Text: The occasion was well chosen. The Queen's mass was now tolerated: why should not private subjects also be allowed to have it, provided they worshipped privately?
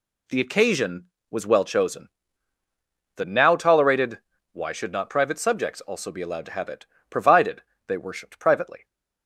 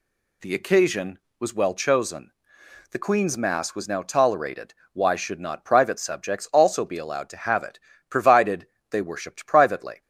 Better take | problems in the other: second | skips "Queen's mass was"; at 3.2 s // pauses between "provided" and "they"; slight; at 7.6 s; 0.26 s long; slight in the second

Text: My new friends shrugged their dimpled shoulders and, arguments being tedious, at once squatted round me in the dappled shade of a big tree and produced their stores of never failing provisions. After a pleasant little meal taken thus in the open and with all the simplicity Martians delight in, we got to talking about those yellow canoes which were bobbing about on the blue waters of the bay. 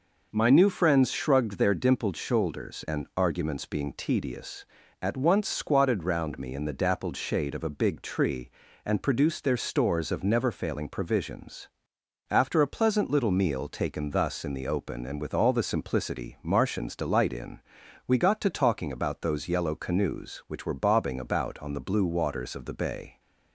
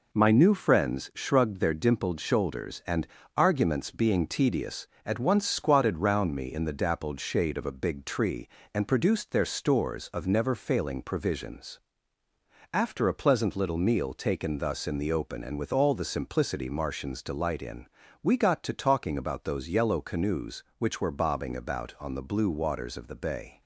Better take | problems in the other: neither | none

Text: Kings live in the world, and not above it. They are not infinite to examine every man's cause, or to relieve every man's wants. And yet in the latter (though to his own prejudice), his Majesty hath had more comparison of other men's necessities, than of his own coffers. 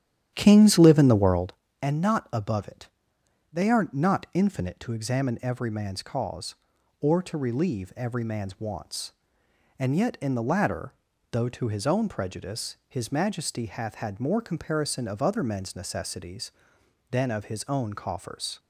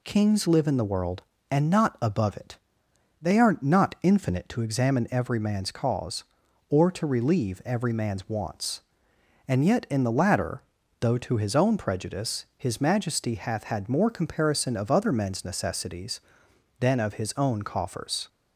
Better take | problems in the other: second | starts louder than the rest; strong; until 1.5 s; 10.5 dB

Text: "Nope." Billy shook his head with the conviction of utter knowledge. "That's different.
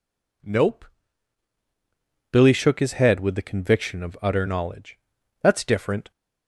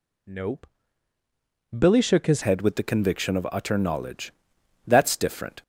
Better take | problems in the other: first | changes voice at "head"; from 2.4 s on; 3.2 s long

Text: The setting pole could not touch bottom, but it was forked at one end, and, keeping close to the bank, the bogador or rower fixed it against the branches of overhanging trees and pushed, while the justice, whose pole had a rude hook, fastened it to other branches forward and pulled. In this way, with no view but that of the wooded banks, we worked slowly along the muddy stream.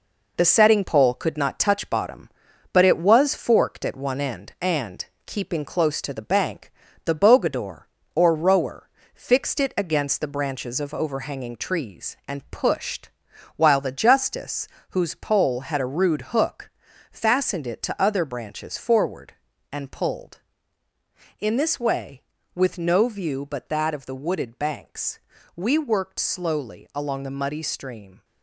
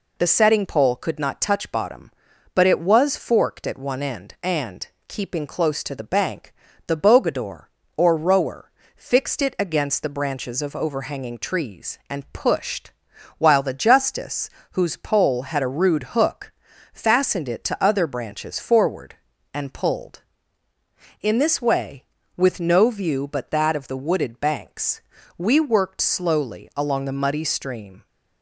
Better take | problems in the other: second | gets quieter; noticeable; throughout; 6 dB // pauses between "rower" and "fixed"; slight; at 8.8 s; 0.24 s long; slight in the second

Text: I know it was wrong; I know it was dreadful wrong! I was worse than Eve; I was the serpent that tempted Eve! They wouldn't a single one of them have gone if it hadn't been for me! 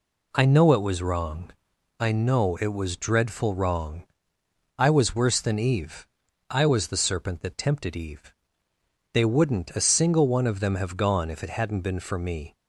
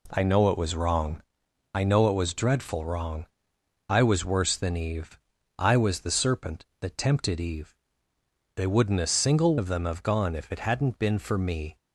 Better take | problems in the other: first | skips "one"; at 9.5 s

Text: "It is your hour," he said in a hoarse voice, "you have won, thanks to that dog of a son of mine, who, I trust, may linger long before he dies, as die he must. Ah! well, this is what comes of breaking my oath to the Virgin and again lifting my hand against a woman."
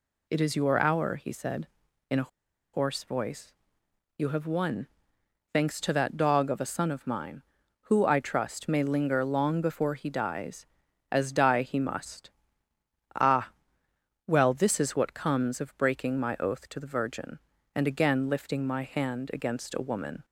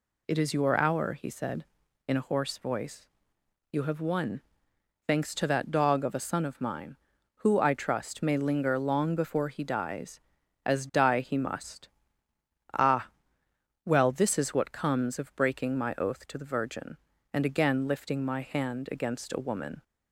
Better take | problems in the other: second | pauses between "a" and "hoarse"; at 2.2 s; 0.44 s long

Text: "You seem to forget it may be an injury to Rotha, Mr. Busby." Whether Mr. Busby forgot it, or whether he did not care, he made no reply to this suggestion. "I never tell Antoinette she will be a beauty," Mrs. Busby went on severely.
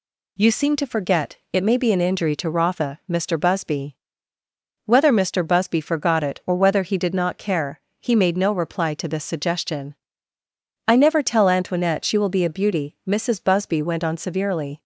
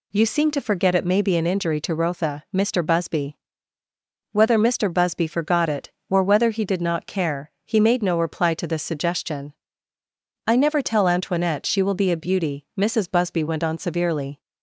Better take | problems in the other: neither | none

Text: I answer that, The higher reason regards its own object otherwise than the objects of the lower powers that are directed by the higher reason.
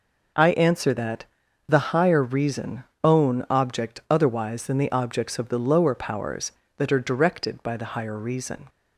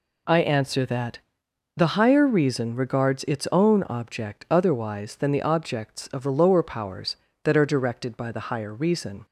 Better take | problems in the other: second | skips "regards its"; at 2.9 s

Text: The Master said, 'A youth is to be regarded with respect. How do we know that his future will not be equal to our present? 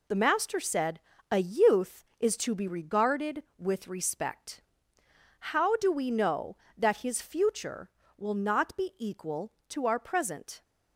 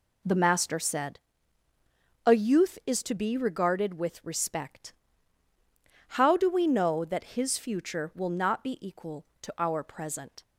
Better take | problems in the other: neither | none

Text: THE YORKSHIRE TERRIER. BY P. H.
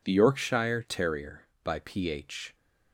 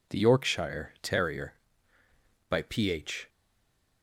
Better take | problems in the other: first | stays silent after the last word; slight; from 3.2 s on; 0.8 s long

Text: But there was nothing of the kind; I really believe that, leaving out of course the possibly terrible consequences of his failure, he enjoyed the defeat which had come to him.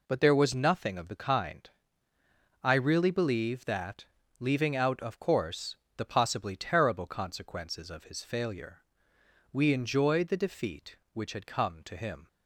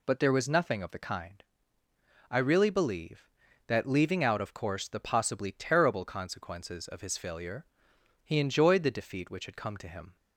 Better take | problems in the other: second | pauses between "course" and "the"; slight; at 5.7 s; 0.20 s long // says "we" for "he"; at 9.5 s

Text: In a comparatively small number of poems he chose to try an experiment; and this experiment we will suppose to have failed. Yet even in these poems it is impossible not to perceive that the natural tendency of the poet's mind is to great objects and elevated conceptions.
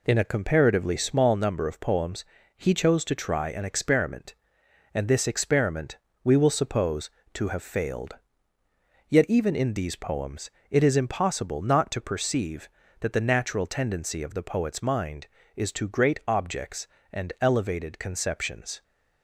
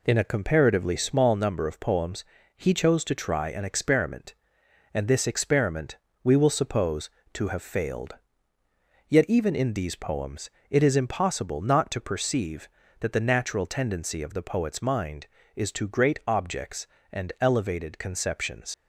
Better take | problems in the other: first | pauses between "poems" and "he"; slight; at 2.2 s; 0.32 s long; slight in the first // pauses between "experiment" and "we"; slight; at 5.9 s; 0.26 s long; slight in the first // pauses between "poems" and "it"; slight; at 10.5 s; 0.18 s long; slight in the first // leaves "conceptions" unfinished; at 18.7 s; 85 ms

